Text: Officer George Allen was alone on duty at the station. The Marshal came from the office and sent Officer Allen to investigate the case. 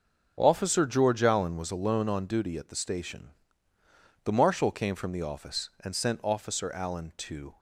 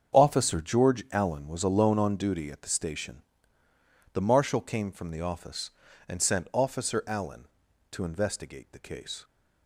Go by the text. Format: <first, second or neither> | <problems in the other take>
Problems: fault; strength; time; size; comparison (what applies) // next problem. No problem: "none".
second | starts louder than the rest; until 1.4 s; 6 dB; strong in the second // stops before "investigate the case"; at 7.5 s